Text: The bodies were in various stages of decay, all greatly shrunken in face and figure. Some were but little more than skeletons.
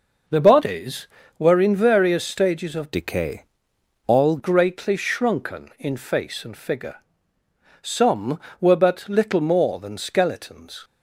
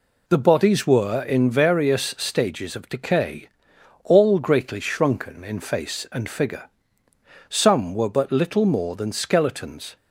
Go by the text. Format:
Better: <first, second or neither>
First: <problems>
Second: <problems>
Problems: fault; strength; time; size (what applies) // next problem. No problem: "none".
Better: second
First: changes voice from "decay" to "all"; from 2.9 to 4.3 s; 1.4 s long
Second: none